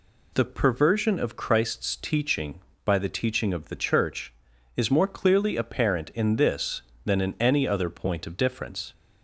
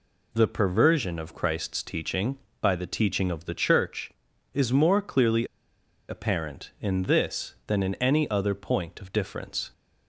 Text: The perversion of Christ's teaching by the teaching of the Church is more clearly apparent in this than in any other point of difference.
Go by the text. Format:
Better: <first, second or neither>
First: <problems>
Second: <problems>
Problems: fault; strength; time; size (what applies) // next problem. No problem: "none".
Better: first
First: none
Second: pauses between "clearly" and "apparent"; noticeable; at 5.4 s; 0.63 s long